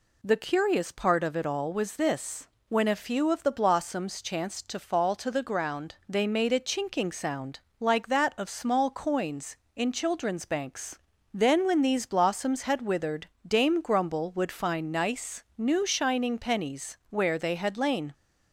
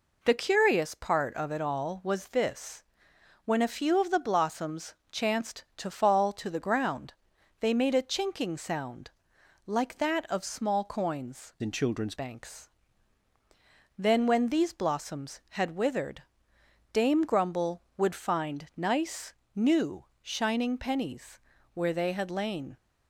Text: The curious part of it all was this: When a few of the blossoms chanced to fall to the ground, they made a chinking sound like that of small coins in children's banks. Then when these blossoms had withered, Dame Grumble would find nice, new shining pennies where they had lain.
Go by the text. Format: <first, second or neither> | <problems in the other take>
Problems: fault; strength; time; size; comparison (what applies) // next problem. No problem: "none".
first | pauses between "blossoms" and "chanced"; slight; at 4.9 s; 0.16 s long // pauses between "sound" and "like"; noticeable; at 9.0 s; 0.56 s long; slight in the first // changes voice from "in" to "children's"; from 11.6 to 12.1 s; 0.5 s long // pauses between "new" and "shining"; slight; at 20.0 s; 0.18 s long // pauses between "pennies" and "where"; slight; at 21.4 s; 0.34 s long